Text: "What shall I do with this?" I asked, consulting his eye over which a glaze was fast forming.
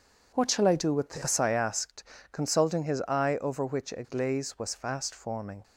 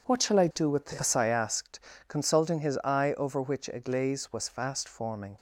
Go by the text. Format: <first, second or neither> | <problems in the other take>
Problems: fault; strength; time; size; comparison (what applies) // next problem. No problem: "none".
neither | none